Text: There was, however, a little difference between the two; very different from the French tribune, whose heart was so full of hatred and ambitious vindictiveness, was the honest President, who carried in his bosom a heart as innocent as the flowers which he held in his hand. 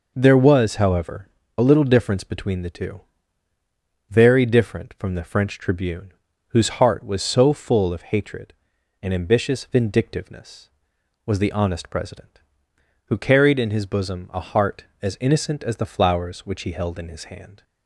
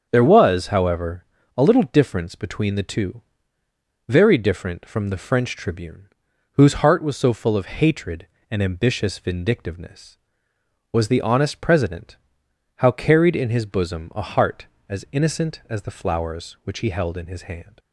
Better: first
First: none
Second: starts louder than the rest; strong; until 1.1 s; 7 dB // says "how" for "who"; at 12.7 s

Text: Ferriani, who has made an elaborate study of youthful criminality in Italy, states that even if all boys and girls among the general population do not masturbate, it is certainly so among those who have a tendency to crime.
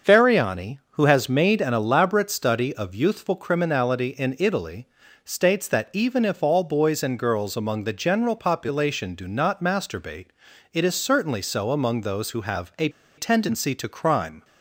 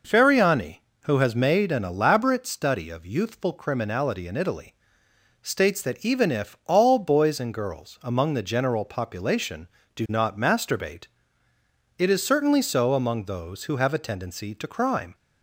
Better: second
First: starts louder than the rest; until 1.1 s; 6.5 dB // pauses between "a" and "tendency"; slight; at 12.8 s; 0.28 s long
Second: none

